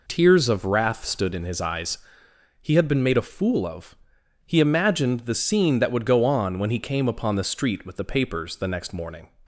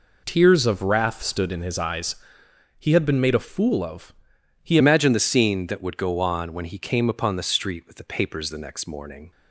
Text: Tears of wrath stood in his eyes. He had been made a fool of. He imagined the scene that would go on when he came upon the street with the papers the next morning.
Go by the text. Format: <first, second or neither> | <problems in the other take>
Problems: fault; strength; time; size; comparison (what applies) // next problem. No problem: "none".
first | changes voice at "imagined"; from 4.7 s on; 4.6 s long